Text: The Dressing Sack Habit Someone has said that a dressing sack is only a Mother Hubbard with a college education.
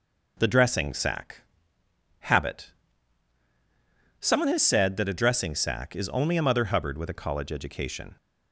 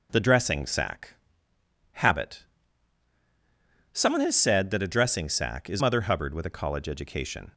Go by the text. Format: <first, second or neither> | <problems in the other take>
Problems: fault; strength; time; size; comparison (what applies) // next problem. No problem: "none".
first | pauses between "Sack" and "Habit"; noticeable; at 1.1 s; 0.78 s long; noticeable in the first // pauses between "Habit" and "Someone"; strong; at 2.4 s; 1.5 s long; strong in the first // skips "only a"; at 5.8 s